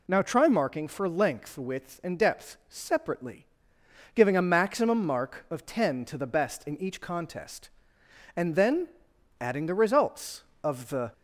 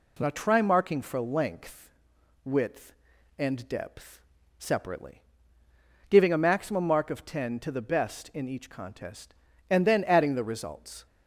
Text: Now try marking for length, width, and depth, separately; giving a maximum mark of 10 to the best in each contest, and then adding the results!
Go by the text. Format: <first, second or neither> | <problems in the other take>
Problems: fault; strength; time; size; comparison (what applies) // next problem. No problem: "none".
second | pauses between "then" and "adding"; noticeable; at 8.8 s; 0.52 s long // goes on to say "Of the"; slight; from 10.6 s on; 0.48 s long